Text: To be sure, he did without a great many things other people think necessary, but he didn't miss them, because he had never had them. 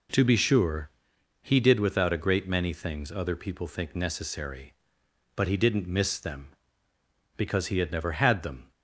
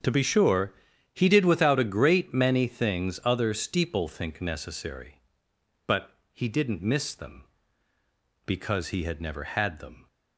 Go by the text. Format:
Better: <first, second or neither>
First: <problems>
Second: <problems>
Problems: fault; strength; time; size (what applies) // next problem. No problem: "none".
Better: first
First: none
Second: starts louder than the rest; strong; until 1.4 s; 7.5 dB // says "steeple" for "people"; at 3.5 s // pauses between "but" and "he"; slight; at 6.1 s; 0.16 s long